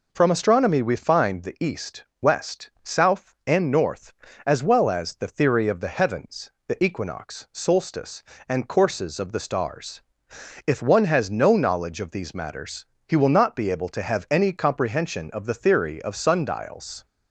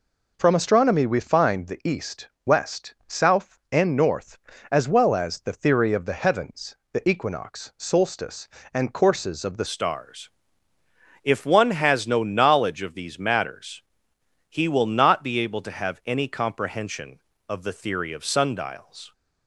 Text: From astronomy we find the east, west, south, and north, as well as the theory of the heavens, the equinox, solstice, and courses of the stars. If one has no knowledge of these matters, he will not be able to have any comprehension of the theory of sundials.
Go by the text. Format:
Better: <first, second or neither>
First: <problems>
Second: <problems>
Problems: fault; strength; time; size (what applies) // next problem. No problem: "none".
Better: first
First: none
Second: changes voice at "stars"; from 9.6 s on; 9.5 s long